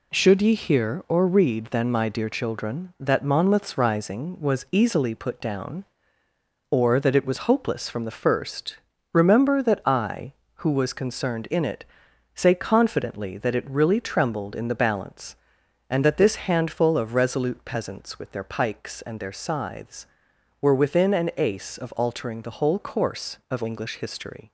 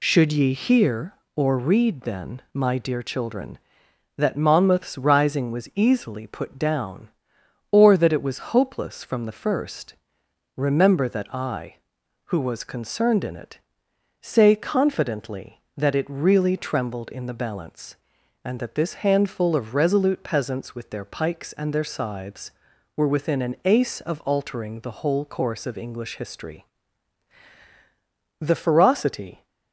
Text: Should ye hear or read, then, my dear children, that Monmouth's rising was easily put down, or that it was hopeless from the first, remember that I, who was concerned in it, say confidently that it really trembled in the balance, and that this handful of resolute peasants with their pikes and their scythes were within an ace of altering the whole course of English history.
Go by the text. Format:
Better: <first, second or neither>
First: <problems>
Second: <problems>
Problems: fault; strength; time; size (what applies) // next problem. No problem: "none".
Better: first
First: none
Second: goes on to say "The ferocity"; noticeable; from 28.4 s on; 1.0 s long